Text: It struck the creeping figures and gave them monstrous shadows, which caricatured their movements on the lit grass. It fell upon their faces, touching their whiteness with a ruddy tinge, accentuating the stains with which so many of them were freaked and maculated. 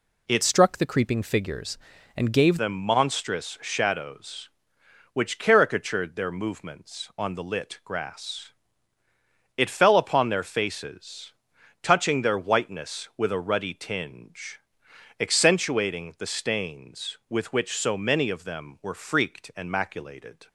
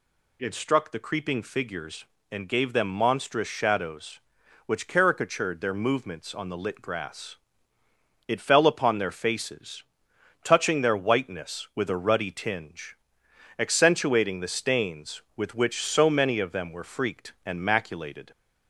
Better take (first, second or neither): second